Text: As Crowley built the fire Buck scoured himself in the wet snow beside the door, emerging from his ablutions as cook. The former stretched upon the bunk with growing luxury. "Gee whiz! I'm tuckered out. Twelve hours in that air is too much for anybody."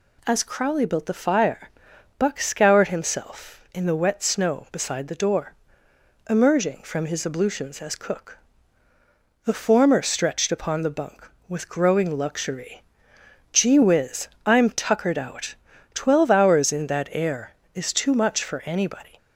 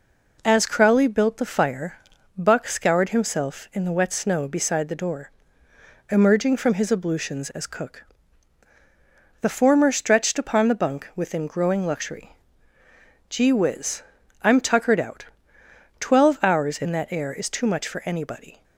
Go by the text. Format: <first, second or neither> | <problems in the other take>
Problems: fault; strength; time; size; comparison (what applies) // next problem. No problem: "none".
first | pauses between "fire" and "Buck"; at 1.9 s; 0.40 s long; noticeable in the first // says "within" for "with"; at 11.1 s